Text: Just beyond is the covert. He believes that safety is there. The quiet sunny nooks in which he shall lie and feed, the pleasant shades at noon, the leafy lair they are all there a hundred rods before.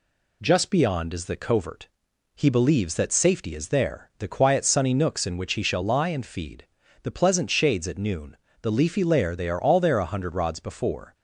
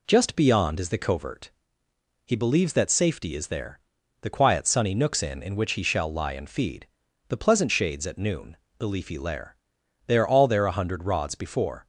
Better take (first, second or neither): first